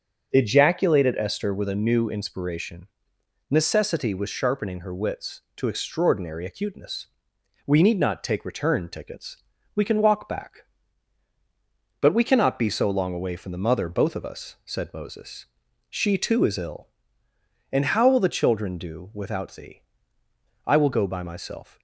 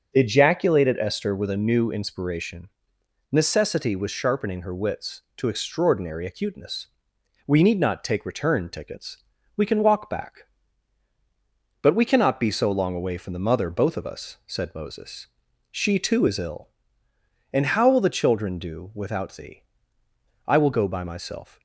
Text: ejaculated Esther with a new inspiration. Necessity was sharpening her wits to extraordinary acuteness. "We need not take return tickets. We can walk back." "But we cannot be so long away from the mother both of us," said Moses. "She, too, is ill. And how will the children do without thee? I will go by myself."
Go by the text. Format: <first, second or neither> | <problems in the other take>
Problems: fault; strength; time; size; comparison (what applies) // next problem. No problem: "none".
neither | starts louder than the rest; the same in both